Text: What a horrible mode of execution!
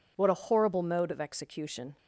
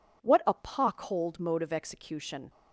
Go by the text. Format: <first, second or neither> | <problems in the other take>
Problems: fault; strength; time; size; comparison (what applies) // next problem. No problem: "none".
first | says "pockholed" for "horrible"; at 0.5 s